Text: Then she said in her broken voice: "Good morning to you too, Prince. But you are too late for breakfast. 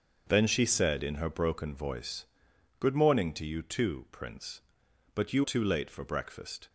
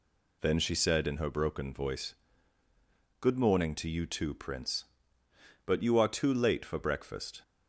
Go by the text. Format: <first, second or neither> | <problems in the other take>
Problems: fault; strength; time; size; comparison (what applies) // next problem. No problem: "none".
second | starts louder than the rest; until 1.2 s; 6.5 dB // skips "are"; at 5.4 s